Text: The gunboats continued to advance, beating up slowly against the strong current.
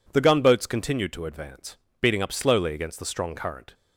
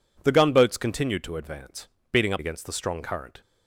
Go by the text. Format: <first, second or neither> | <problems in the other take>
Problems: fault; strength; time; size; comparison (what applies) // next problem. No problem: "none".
first | skips "slowly"; at 2.3 s